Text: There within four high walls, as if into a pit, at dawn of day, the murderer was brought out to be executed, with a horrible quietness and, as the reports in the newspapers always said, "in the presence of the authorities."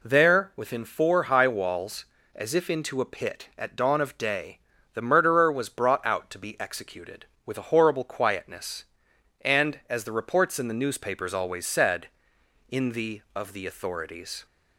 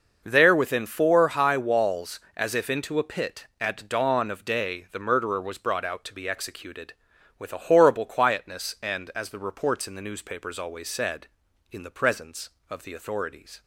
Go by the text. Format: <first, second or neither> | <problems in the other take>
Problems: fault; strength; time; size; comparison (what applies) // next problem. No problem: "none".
second | skips "presence"; at 13.2 s